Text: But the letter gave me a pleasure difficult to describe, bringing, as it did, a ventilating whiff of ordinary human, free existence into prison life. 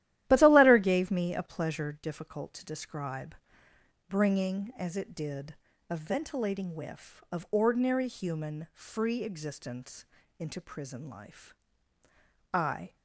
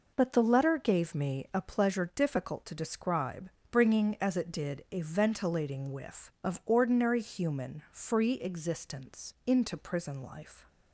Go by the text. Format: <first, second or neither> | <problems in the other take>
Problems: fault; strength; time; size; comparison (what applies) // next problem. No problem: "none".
second | starts louder than the rest; strong; until 1.2 s; 13.5 dB // pauses between "existence" and "into"; slight; at 10.0 s; 0.34 s long // goes on to say "I"; slight; from 12.5 s on; 0.42 s long